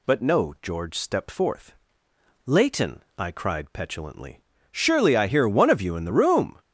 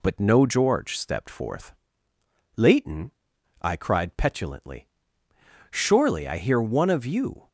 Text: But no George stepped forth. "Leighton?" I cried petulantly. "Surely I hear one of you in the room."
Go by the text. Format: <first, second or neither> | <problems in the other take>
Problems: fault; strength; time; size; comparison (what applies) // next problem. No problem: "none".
first | stops before "in the room"; at 7.4 s